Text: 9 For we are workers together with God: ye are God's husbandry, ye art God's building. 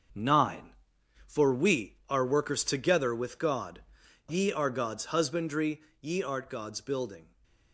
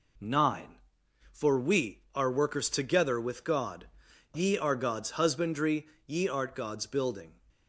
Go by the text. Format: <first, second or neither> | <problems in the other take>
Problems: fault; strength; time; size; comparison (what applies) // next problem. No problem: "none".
second | gets quieter; noticeable; throughout; 6 dB